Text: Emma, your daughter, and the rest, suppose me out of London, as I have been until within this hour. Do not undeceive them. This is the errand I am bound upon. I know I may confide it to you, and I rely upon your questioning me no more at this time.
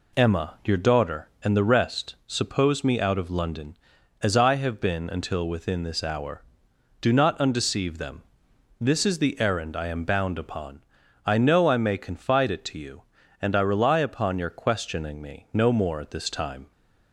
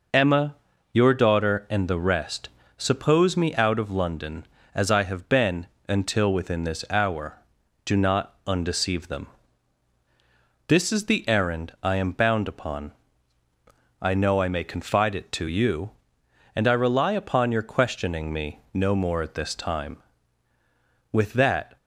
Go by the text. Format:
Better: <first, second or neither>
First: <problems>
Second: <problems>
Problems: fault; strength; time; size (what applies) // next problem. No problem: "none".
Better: first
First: none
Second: pauses between "been" and "until"; slight; at 5.6 s; 0.20 s long // goes on to say "With that"; noticeable; from 21.1 s on; 0.66 s long